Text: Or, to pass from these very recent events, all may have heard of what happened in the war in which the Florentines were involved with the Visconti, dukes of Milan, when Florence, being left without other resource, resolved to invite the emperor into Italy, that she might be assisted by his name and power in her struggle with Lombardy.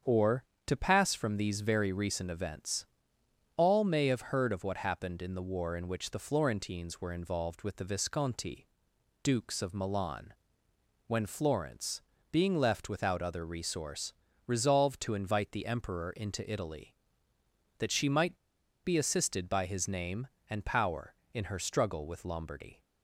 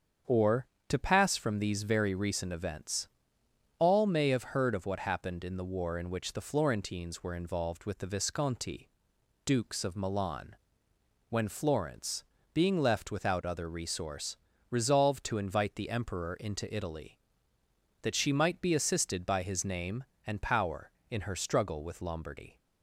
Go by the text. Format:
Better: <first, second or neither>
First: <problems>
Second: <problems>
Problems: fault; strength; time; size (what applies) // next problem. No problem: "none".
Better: second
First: starts louder than the rest; strong; until 1.2 s; 7.5 dB // pauses between "might" and "be"; noticeable; at 18.3 s; 0.47 s long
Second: starts louder than the rest; strong; until 1.4 s; 7.5 dB